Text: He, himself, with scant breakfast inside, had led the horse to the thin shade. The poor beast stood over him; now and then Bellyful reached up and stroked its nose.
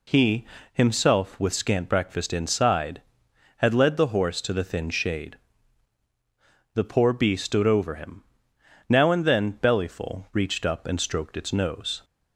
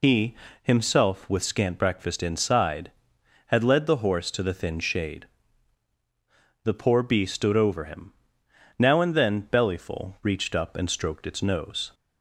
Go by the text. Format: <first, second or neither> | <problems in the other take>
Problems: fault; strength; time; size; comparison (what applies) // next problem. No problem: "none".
first | loses the start of "He"; at 0.0 s; 60 ms